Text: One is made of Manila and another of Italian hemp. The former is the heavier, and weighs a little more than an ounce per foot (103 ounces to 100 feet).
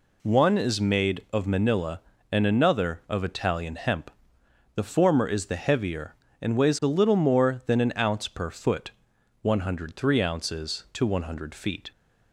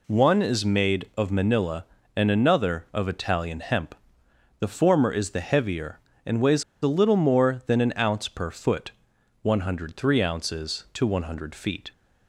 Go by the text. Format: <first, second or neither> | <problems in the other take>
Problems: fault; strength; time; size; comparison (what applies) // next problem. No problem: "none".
first | pauses between "weighs" and "a"; slight; at 6.6 s; 0.20 s long